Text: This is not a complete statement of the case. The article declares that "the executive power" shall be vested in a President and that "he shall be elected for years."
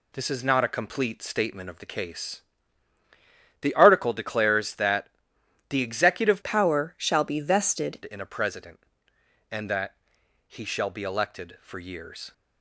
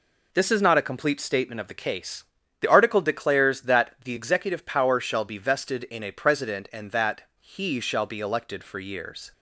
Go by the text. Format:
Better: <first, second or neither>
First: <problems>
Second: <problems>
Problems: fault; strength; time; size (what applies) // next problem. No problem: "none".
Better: second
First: pauses between "that" and "the"; noticeable; at 5.0 s; 0.60 s long // changes voice from "power" to "vested"; from 6.4 to 7.9 s; 1.5 s long // pauses between "that" and "he"; noticeable; at 9.9 s; 0.52 s long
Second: pauses between "that" and "he"; slight; at 7.2 s; 0.18 s long